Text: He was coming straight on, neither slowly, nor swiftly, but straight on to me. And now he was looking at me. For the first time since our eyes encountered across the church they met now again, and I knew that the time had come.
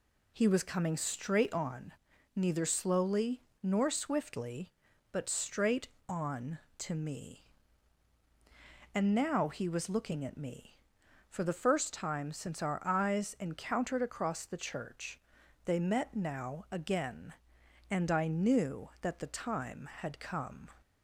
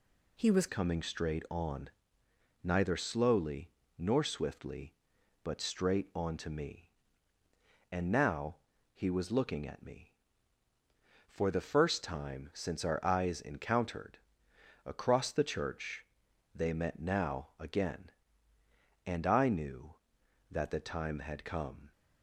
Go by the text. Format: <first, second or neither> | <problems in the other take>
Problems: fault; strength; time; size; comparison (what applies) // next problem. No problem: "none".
first | changes voice at "coming"; from 0.6 s on; 21.3 s long // pauses between "now" and "he"; at 8.5 s; 0.38 s long // pauses between "encountered" and "across"; noticeable; at 14.1 s; 0.66 s long // pauses between "church" and "they"; noticeable; at 16.0 s; 0.50 s long; noticeable in the first